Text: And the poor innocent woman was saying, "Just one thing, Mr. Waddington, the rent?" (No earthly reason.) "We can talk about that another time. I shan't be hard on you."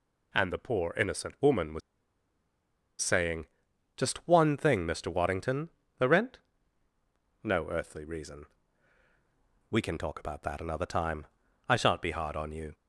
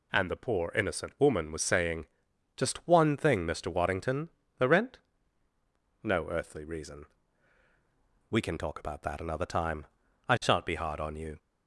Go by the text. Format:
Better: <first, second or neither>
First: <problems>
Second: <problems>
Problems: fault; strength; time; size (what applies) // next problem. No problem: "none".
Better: second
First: pauses between "was" and "saying"; at 1.8 s; 1.2 s long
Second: none